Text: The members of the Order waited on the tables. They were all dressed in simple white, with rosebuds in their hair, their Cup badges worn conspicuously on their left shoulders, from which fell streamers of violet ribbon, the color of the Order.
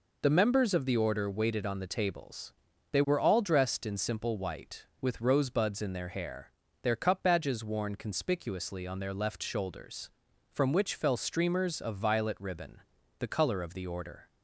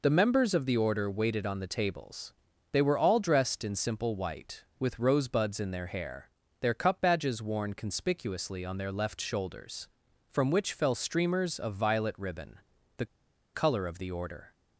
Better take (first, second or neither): first